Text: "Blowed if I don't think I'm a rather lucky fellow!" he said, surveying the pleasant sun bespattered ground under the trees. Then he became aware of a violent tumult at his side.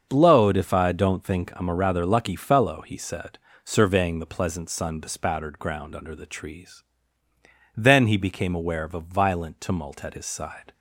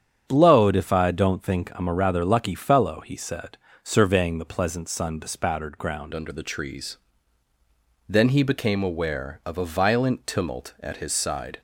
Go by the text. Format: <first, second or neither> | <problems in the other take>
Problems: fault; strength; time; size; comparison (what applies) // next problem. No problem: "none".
first | starts louder than the rest; strong; until 1.2 s; 8.5 dB; also in the first // changes voice at "under"; from 6.1 s on; 5.5 s long